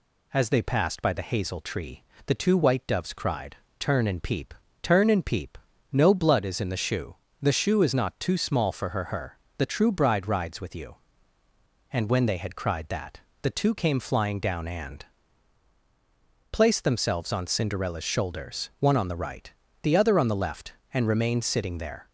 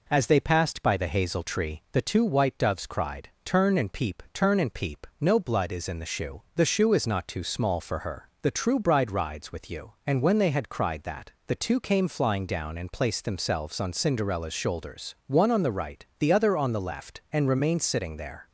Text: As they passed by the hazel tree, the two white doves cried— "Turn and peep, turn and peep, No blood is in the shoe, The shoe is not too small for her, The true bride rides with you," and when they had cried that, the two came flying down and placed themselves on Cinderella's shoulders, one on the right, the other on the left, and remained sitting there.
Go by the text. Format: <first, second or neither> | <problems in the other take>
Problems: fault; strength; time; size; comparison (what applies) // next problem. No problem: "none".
second | says "her" twice; at 9.0 s // pauses between "and" and "placed"; strong; at 15.0 s; 1.4 s long